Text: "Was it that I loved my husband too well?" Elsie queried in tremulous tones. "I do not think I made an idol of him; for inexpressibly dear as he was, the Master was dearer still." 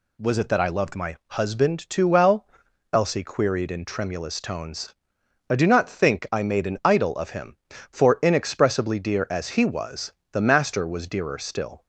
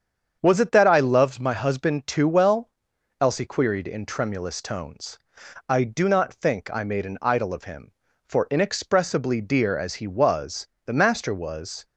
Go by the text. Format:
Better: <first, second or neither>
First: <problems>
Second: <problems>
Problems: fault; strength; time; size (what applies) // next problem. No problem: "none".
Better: first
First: none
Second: starts louder than the rest; strong; until 1.4 s; 7.5 dB // stops before "dearer still"; at 11.8 s